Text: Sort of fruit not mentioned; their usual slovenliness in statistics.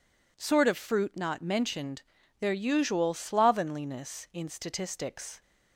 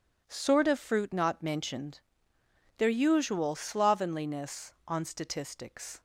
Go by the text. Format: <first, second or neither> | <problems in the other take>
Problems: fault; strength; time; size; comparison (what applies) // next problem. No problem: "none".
first | says "on" for "in"; at 4.8 s